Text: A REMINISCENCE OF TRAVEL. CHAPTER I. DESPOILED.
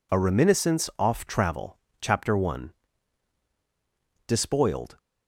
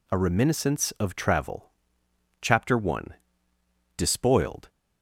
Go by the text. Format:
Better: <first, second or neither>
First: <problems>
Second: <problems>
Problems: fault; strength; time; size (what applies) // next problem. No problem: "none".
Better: second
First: says "Off" for "OF"; at 0.9 s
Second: none